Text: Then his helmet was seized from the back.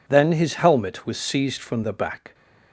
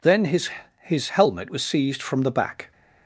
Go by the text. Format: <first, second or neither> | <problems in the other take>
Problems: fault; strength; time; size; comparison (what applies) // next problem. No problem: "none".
first | says "his" twice; at 0.8 s